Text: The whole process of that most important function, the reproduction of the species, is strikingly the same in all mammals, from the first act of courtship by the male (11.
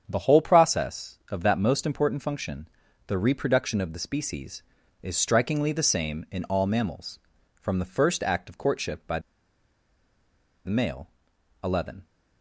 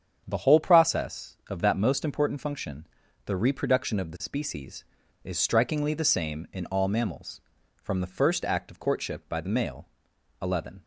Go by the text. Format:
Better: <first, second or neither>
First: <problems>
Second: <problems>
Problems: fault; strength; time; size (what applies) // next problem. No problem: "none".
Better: second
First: starts louder than the rest; strong; until 1.0 s; 8 dB // pauses between "by" and "the"; strong; at 9.1 s; 1.4 s long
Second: starts louder than the rest; strong; until 1.2 s; 8 dB